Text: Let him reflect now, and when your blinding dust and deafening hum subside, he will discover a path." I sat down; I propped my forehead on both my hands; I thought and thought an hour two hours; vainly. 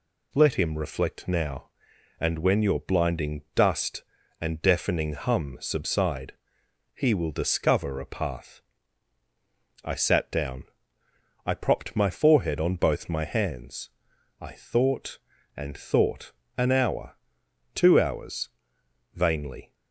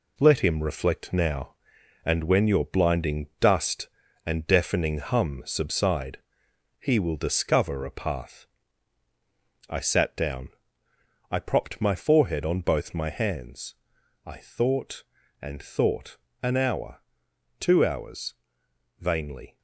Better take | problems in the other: first | gets quieter; throughout; 6 dB // pauses between "thought" and "an"; slight; at 16.1 s; 0.26 s long; slight in the first // pauses between "hour" and "two"; noticeable; at 17.0 s; 0.58 s long; noticeable in the first

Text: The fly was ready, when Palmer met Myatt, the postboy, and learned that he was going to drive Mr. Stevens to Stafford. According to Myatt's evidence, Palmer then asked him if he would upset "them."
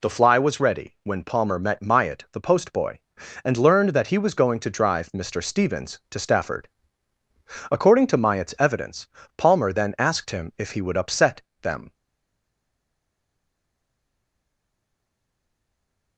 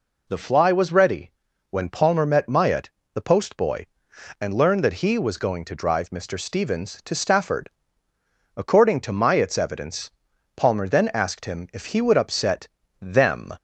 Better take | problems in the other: second | pauses between "upset" and "them"; slight; at 11.4 s; 0.22 s long; slight in the second // stays silent after the last word; strong; from 11.9 s on; 4.2 s long

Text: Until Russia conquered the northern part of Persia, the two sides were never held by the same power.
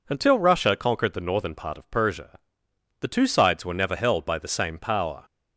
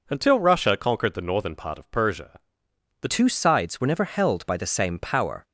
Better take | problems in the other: first | changes voice at "two"; from 3.0 s on; 2.4 s long

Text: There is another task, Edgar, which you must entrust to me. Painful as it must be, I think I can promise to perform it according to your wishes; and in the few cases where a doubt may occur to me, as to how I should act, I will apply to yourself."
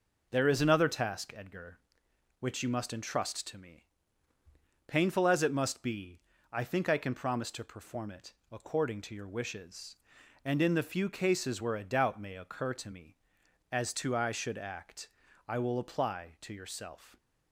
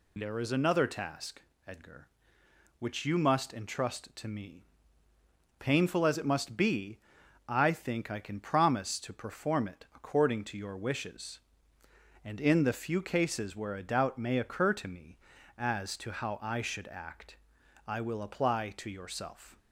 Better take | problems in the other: second | pauses between "it" and "according"; slight; at 8.3 s; 0.18 s long // skips "how"; at 14.1 s

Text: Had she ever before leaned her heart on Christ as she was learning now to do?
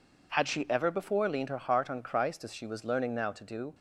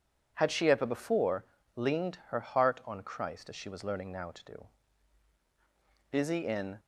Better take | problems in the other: first | pauses between "before" and "leaned"; slight; at 1.4 s; 0.30 s long // goes on to say "Busy in"; noticeable; from 6.0 s on; 0.70 s long

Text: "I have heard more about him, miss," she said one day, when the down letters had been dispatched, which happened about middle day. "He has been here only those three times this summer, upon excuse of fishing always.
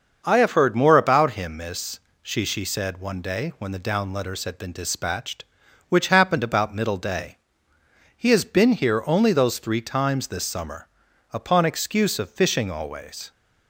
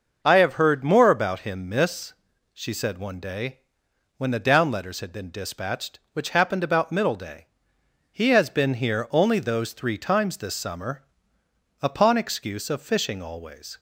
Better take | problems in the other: second | starts louder than the rest; until 1.2 s; 6.5 dB; also in the second // says "she" twice; at 2.4 s

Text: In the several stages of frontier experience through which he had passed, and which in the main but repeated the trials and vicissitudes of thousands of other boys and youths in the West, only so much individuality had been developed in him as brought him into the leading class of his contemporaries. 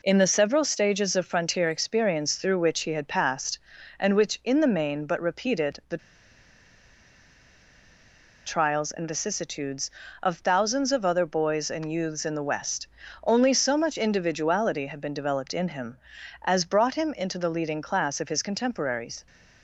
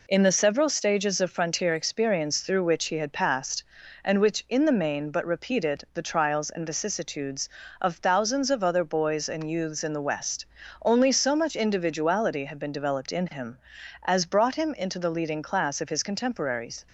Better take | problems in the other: second | pauses between "the" and "trials"; strong; at 5.9 s; 2.4 s long

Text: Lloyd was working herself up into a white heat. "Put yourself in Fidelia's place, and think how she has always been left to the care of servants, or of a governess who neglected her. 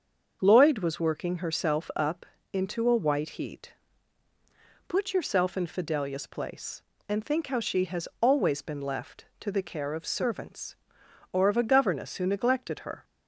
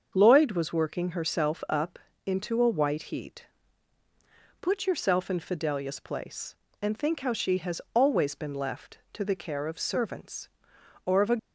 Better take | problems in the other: first | starts louder than the rest; until 1.1 s; 6.5 dB; also in the first // pauses between "up" and "into"; slight; at 1.9 s; 0.28 s long; slight in the first // stops before "governess who neglected her"; at 11.3 s

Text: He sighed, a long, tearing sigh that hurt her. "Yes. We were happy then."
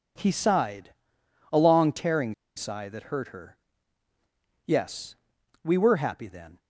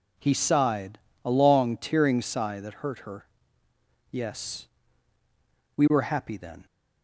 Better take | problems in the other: second | pauses between "tearing" and "sigh"; slight; at 2.3 s; 0.23 s long

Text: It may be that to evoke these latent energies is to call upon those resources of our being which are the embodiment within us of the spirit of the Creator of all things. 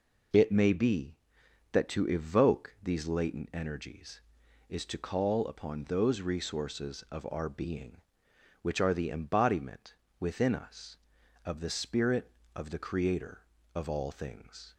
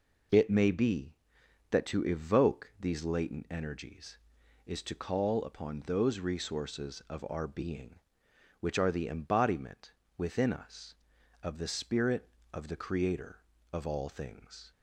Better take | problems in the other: neither | pauses between "embodiment" and "within"; slight; the same in both

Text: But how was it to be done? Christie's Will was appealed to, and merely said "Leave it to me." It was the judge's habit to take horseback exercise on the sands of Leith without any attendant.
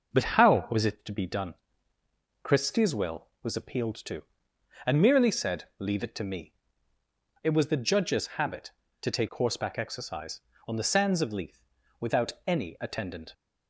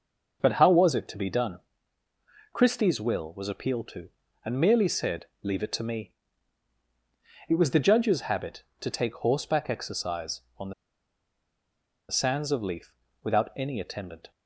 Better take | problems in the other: first | starts louder than the rest; until 1.4 s; 6 dB // pauses between "said" and "Leave"; slight; at 5.2 s; 0.16 s long; slight in the first // pauses between "on" and "the"; strong; at 10.7 s; 1.3 s long // pauses between "Leith" and "without"; slight; at 12.9 s; 0.28 s long; slight in the first

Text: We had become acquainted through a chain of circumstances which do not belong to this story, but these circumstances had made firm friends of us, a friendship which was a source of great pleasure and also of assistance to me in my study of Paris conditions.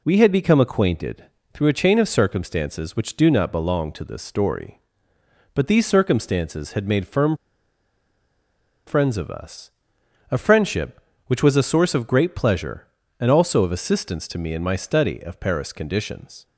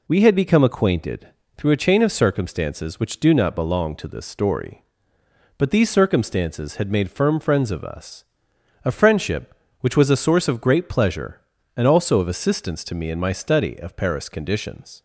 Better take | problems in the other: second | pauses between "acquainted" and "through"; slight; at 1.2 s; 0.28 s long; slight in the second // pauses between "firm" and "friends"; strong; at 7.3 s; 1.5 s long

